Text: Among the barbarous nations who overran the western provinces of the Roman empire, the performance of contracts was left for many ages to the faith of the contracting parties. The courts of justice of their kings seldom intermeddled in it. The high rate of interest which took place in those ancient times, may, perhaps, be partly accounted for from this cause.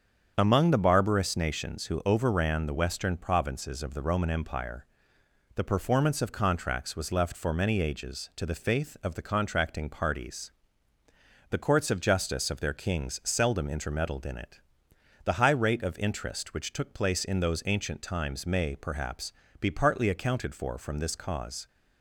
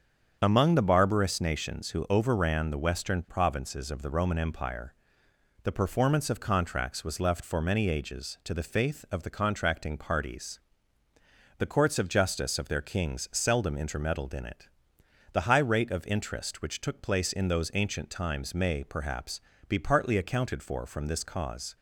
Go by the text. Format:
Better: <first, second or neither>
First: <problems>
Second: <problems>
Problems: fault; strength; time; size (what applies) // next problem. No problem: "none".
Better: neither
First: starts louder than the rest; strong; until 1.3 s; 7.5 dB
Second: starts louder than the rest; strong; until 1.4 s; 7.5 dB